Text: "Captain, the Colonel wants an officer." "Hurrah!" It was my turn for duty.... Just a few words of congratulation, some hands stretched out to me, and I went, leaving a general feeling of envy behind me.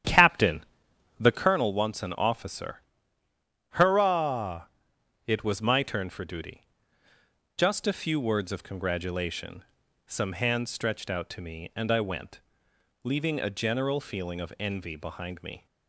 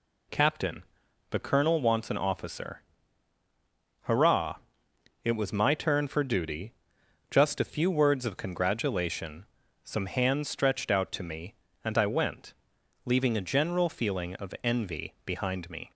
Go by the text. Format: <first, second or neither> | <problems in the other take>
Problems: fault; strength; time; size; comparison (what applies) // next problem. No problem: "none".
second | starts louder than the rest; strong; until 1.5 s; 10 dB